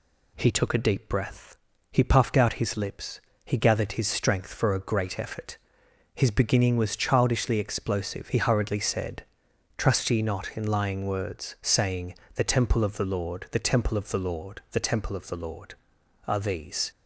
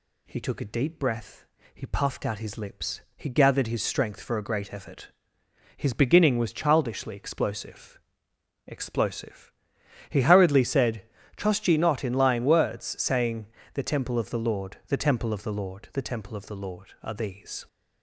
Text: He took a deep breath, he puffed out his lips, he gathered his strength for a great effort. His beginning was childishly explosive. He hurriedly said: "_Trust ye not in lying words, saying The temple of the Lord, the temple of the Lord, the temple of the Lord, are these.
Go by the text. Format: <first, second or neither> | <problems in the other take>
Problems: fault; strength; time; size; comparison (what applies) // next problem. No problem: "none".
first | says "explosive" twice; at 8.6 s // pauses between "saying" and "The"; slight; at 13.4 s; 0.28 s long; slight in the first